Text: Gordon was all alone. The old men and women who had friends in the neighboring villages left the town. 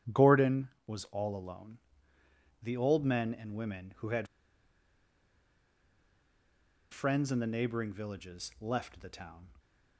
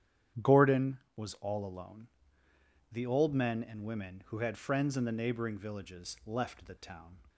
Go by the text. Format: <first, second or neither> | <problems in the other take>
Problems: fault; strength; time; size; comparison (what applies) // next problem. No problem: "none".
second | starts louder than the rest; strong; until 1.3 s; 9.5 dB; strong in the second // pauses between "had" and "friends"; strong; at 4.2 s; 2.6 s long